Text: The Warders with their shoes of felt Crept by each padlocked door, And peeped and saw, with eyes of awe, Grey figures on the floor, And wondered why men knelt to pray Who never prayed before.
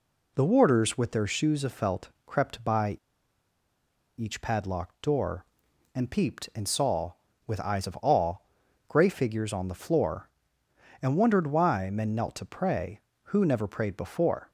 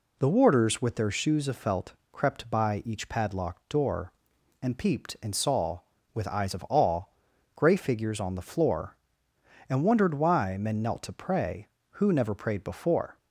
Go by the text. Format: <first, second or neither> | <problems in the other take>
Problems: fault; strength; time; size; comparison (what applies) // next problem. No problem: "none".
second | pauses between "felt" and "Crept"; slight; at 2.0 s; 0.18 s long; slight in the second // pauses between "by" and "each"; at 2.9 s; 1.2 s long